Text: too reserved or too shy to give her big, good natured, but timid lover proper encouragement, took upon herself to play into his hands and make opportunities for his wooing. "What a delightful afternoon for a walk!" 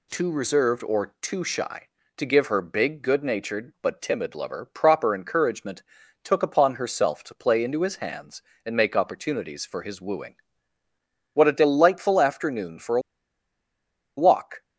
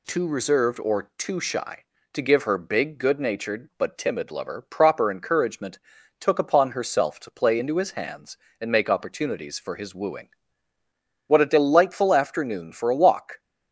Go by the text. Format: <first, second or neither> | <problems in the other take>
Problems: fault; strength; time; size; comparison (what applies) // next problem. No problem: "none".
second | pauses between "a" and "walk"; at 13.0 s; 1.1 s long